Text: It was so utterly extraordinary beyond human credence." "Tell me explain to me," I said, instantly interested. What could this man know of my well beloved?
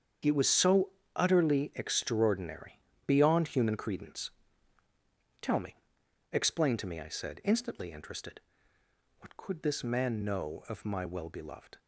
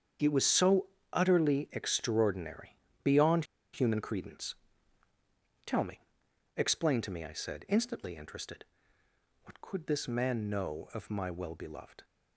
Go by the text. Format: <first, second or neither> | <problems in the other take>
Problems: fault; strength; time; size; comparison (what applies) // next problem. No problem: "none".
first | starts louder than the rest; strong; until 1.5 s; 7.5 dB; strong in the first // pauses between "so" and "utterly"; slight; at 0.8 s; 0.30 s long; slight in the first // pauses between "extraordinary" and "beyond"; slight; at 2.7 s; 0.26 s long; slight in the first // pauses between "beyond" and "human"; slight; at 3.4 s; 0.28 s long // pauses between "me" and "explain"; noticeable; at 5.9 s; 0.56 s long; noticeable in the first